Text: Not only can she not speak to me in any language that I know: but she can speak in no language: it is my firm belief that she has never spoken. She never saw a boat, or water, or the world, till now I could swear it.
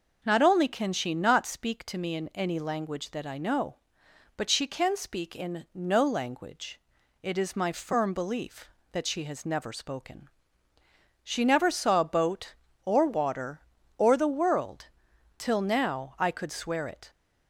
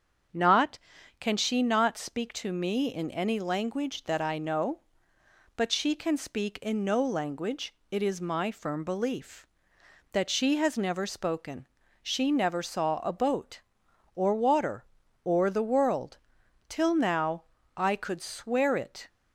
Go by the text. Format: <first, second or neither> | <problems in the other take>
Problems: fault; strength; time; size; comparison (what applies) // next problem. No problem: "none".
first | starts louder than the rest; strong; until 1.7 s; 7 dB // skips "only"; at 0.9 s // pauses between "now" and "I"; slight; at 17.4 s; 0.34 s long